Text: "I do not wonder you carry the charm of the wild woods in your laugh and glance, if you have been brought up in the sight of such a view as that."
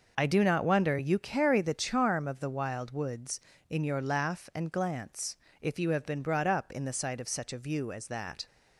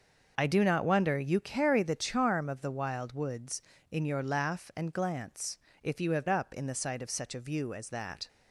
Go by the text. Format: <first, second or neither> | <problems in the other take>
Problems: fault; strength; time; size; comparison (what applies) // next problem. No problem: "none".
first | starts louder than the rest; until 1.3 s; 6 dB // skips "been brought"; at 6.2 s